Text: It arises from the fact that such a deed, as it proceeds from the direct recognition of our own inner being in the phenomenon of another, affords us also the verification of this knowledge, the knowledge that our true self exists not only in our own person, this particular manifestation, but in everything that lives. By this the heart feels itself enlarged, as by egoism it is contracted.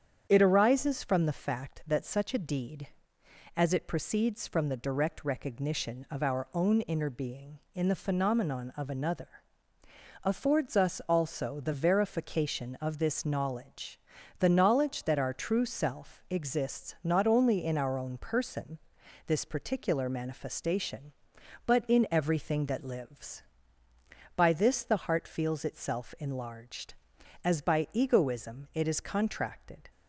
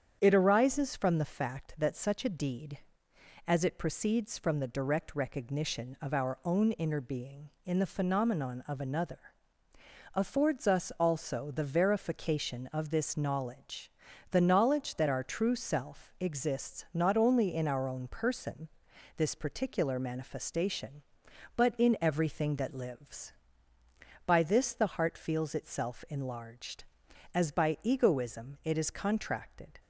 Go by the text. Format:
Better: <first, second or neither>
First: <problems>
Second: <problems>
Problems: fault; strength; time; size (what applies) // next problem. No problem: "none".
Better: neither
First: starts louder than the rest; strong; until 1.3 s; 8 dB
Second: starts louder than the rest; strong; until 1.2 s; 8 dB